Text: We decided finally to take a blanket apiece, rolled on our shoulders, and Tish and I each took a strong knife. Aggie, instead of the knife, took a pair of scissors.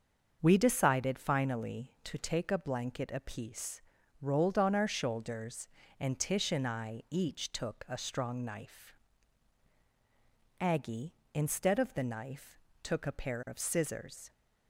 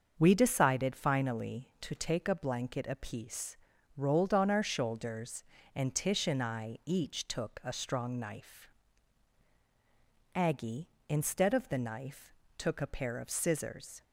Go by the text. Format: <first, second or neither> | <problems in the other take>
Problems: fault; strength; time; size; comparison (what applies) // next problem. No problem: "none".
neither | starts louder than the rest; the same in both